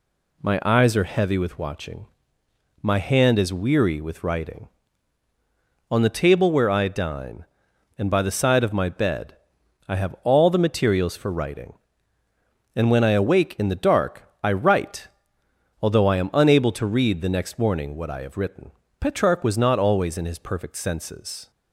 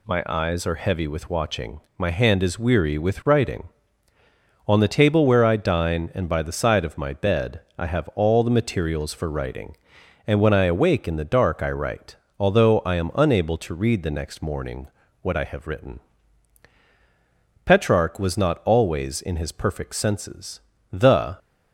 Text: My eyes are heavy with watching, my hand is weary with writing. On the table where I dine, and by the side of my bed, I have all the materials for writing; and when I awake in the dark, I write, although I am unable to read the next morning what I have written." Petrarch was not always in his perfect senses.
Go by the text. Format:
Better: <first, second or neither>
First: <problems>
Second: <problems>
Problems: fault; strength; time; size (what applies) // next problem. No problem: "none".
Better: first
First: none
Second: pauses between "morning" and "what"; slight; at 14.8 s; 0.34 s long // goes on to say "The"; slight; from 20.9 s on; 0.46 s long